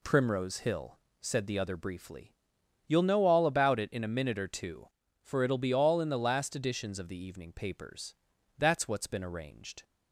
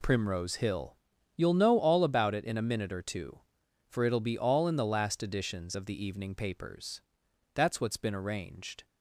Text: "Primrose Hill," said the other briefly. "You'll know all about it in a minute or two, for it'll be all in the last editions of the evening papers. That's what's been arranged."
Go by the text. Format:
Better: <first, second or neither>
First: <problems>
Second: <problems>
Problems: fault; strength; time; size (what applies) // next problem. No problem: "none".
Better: first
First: none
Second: skips "said the other briefly"; at 1.1 s